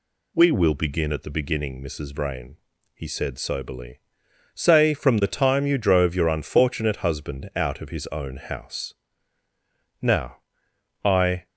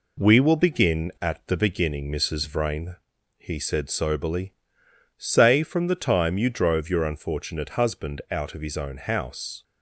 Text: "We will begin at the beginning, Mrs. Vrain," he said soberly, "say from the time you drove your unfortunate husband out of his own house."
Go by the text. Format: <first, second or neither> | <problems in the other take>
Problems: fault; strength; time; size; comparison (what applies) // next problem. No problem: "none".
second | goes on to say "Now I"; from 10.0 s on; 1.4 s long